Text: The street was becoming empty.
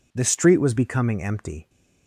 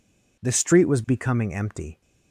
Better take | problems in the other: neither | none

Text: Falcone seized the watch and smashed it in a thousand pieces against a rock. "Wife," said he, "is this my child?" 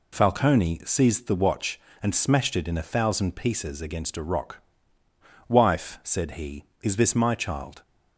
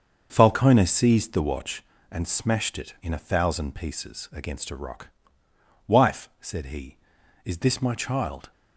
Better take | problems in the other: first | starts louder than the rest; until 1.8 s; 6.5 dB

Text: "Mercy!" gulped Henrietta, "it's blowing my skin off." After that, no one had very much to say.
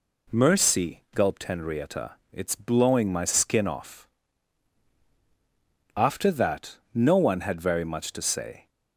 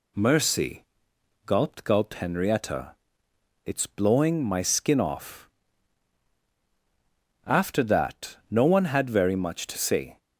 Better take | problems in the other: first | says "gulped" twice; at 1.8 s

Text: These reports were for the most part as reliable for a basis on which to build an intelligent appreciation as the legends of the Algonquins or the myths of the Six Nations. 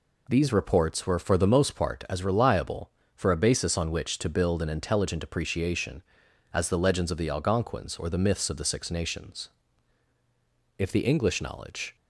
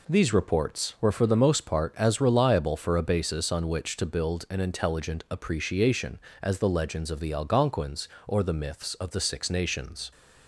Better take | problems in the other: second | goes on to say "If the English knowledge"; noticeable; from 10.7 s on; 1.1 s long

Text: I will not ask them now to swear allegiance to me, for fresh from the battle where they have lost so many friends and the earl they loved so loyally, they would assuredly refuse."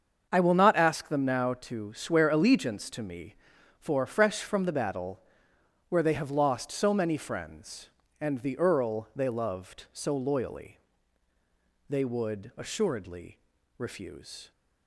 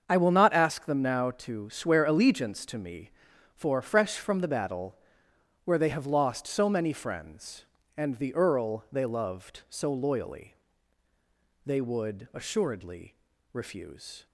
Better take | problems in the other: neither | starts louder than the rest; the same in both // pauses between "battle" and "where"; noticeable; the same in both // pauses between "assuredly" and "refuse"; the same in both

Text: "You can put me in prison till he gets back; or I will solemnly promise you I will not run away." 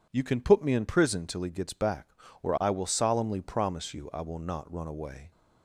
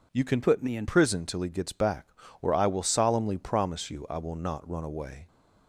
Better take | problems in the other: first | changes voice from "put" to "in"; from 0.4 to 0.8 s; 0.4 s long

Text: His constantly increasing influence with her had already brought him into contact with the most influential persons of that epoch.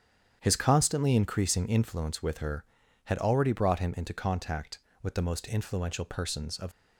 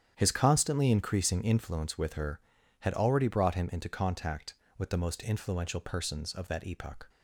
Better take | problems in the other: second | starts louder than the rest; strong; until 1.4 s; 9 dB; strong in the second // stops before "that epoch"; at 6.7 s

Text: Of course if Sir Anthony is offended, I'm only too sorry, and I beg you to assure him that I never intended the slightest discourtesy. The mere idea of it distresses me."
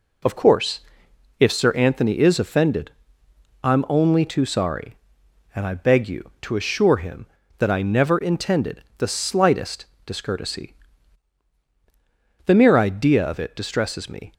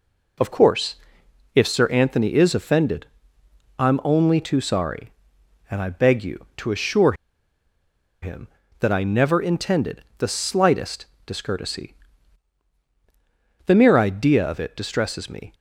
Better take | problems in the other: first | pauses between "course" and "if"; noticeable; at 0.9 s; 0.60 s long; noticeable in the first // pauses between "assure" and "him"; at 7.1 s; 1.0 s long // pauses between "intended" and "the"; slight; at 10.0 s; 0.16 s long; slight in the first // pauses between "slightest" and "discourtesy"; slight; at 11.0 s; 0.22 s long; slight in the first

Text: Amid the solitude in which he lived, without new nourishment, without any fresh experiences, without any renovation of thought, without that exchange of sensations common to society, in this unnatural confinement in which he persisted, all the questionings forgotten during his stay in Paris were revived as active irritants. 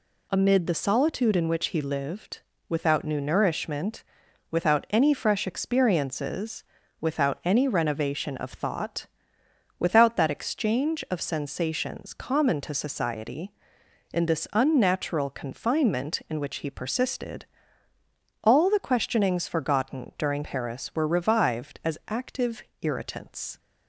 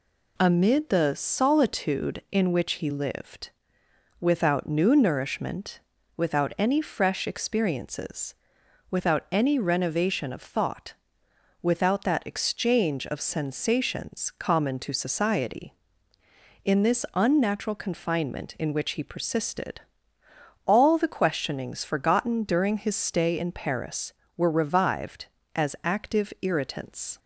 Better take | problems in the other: second | skips "his stay in"; at 20.4 s // pauses between "active" and "irritants"; slight; at 22.6 s; 0.18 s long

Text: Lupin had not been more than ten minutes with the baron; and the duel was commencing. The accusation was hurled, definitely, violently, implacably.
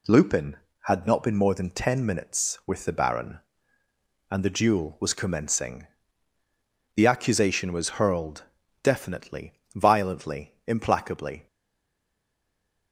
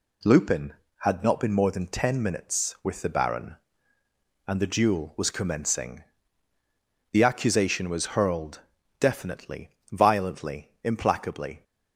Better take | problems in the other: second | stays silent after the last word; noticeable; from 11.4 s on; 1.5 s long

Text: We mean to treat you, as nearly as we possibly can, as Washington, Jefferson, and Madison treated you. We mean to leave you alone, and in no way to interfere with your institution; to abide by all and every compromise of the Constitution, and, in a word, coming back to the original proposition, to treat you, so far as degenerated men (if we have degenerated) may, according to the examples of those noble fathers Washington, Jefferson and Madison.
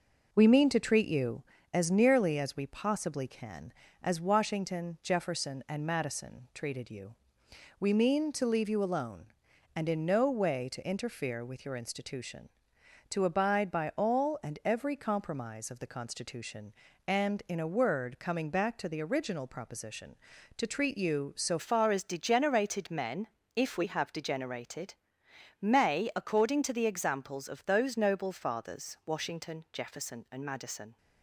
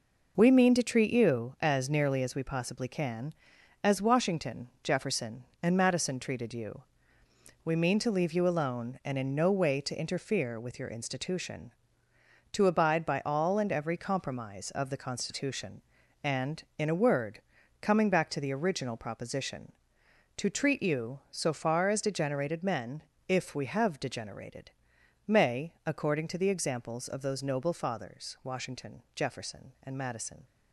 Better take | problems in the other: second | changes voice at "far"; from 21.5 s on; 9.4 s long

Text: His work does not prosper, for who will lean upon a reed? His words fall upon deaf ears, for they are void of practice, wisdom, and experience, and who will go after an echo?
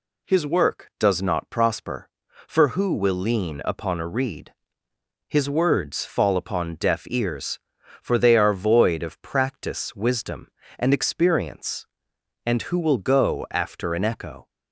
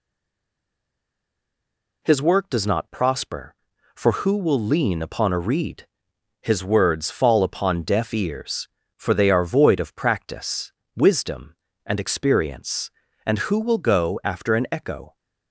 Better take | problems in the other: first | stays silent before the first word; noticeable; until 2.0 s; 2.0 s long

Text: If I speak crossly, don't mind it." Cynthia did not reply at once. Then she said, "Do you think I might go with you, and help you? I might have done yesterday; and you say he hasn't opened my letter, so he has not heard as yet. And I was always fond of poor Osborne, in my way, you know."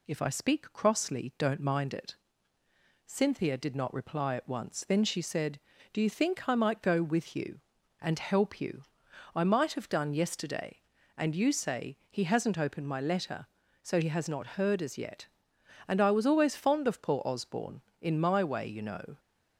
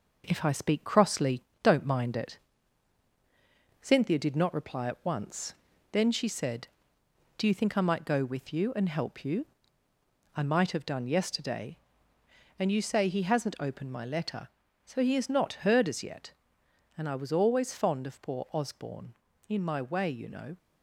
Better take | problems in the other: first | gets quieter; throughout; 3.5 dB

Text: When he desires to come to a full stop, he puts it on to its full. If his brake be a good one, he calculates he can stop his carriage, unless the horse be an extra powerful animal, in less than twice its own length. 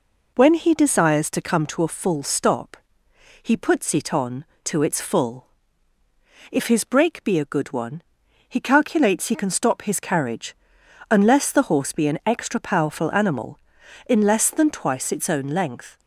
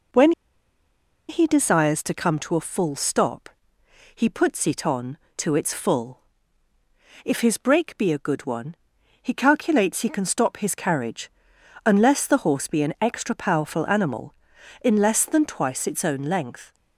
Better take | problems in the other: first | pauses between "When" and "he"; noticeable; at 0.3 s; 0.97 s long

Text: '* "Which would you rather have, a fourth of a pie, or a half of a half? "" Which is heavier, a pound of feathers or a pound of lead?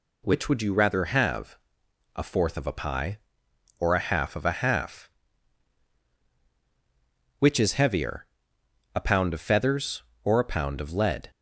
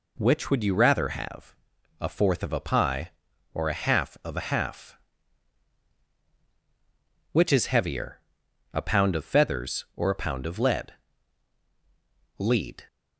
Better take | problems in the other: first | says "lead" twice; at 12.3 s

